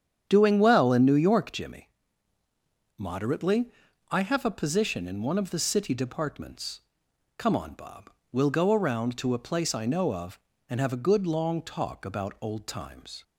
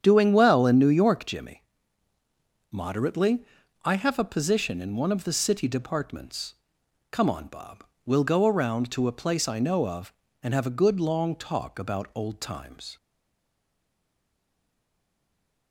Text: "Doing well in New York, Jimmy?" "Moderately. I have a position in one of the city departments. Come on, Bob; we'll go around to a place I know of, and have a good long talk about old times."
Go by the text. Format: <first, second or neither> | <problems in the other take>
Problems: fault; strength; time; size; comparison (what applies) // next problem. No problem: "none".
first | starts louder than the rest; strong; until 1.0 s; 8.5 dB; strong in the first // stays silent after the last word; strong; from 12.9 s on; 2.8 s long